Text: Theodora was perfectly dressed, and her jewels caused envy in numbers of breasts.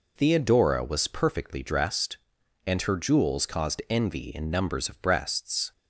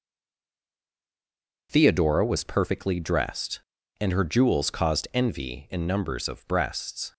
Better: first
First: none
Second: stays silent before the first word; noticeable; until 1.6 s; 1.6 s long

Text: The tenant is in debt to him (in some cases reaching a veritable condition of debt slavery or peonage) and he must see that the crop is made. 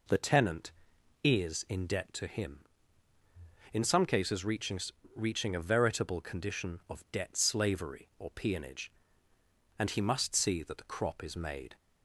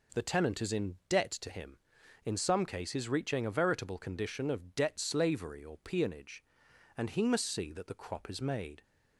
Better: second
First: says "reaching" twice; at 5.1 s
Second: none

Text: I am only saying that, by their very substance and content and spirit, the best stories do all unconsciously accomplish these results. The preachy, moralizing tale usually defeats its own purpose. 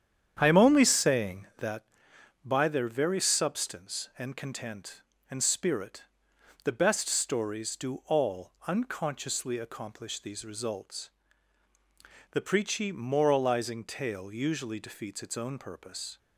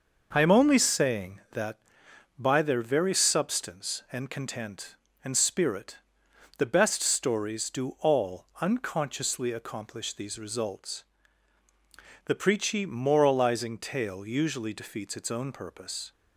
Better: second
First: starts louder than the rest; strong; until 1.8 s; 9 dB // pauses between "all" and "unconsciously"; slight; at 8.5 s; 0.16 s long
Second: pauses between "all" and "unconsciously"; slight; at 8.4 s; 0.16 s long

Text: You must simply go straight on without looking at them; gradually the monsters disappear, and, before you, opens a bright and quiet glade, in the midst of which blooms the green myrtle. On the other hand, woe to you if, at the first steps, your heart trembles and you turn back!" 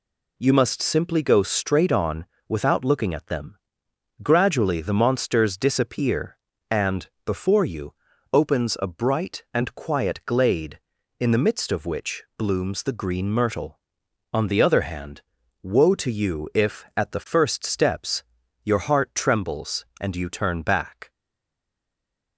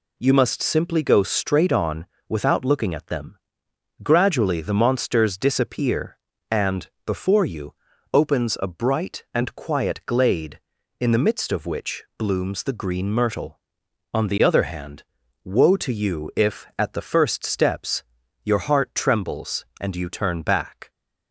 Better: second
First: pauses between "on" and "without"; slight; at 2.2 s; 0.20 s long // stays silent after the last word; noticeable; from 21.1 s on; 1.2 s long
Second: pauses between "on" and "without"; slight; at 2.0 s; 0.20 s long

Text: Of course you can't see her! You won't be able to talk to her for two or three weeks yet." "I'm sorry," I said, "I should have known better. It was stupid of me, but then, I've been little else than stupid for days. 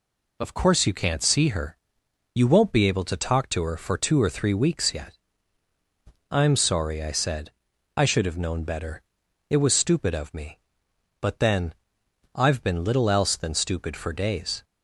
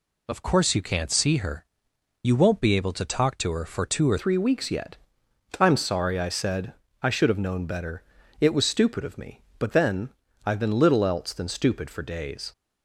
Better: first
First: none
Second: changes voice at "three"; from 4.1 s on; 8.4 s long

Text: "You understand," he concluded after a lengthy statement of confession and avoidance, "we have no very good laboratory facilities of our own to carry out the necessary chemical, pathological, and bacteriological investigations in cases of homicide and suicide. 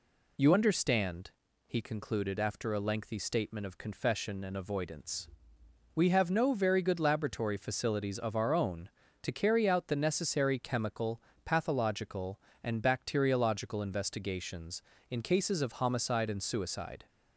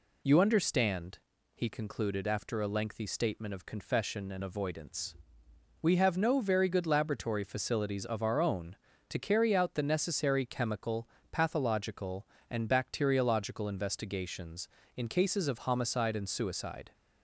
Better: neither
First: none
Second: none

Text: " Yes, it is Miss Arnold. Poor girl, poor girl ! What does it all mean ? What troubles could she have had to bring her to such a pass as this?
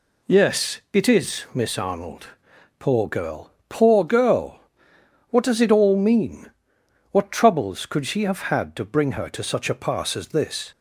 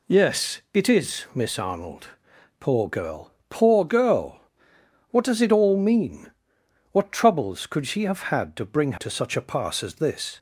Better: first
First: none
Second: skips "her"; at 8.9 s

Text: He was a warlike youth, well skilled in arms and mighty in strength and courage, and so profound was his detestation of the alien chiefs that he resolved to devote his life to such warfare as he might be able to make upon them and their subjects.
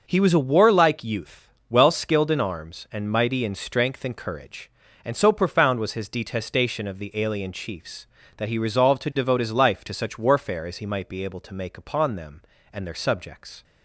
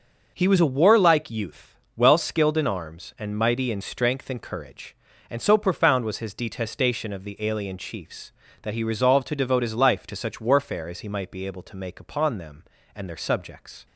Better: neither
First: none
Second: none

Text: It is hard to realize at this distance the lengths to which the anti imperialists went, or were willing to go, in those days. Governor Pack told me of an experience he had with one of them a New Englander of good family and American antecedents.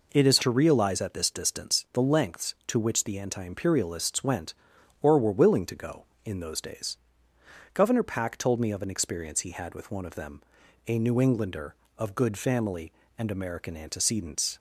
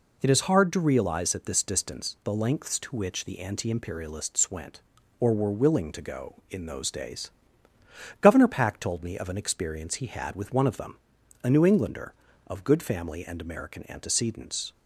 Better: second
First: skips "hard"; at 0.3 s // pauses between "them" and "a"; noticeable; at 10.4 s; 0.46 s long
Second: pauses between "them" and "a"; noticeable; at 10.9 s; 0.46 s long

